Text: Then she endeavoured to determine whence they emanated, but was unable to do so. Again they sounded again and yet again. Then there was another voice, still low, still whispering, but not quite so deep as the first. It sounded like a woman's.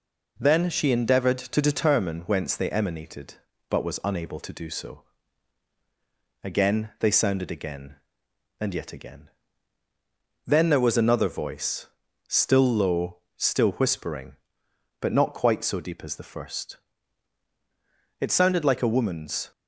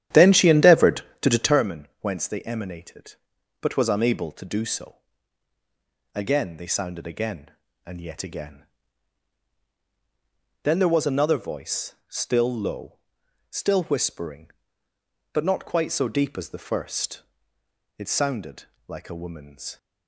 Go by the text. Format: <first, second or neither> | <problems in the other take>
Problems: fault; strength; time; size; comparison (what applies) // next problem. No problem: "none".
first | starts louder than the rest; strong; until 1.7 s; 11 dB // pauses between "sounded" and "like"; slight; at 18.6 s; 0.24 s long